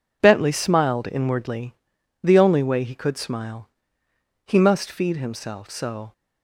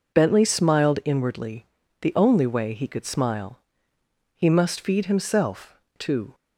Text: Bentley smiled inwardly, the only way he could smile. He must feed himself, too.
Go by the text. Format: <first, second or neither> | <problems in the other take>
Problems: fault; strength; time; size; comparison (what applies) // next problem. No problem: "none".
second | says "so" for "too"; at 5.7 s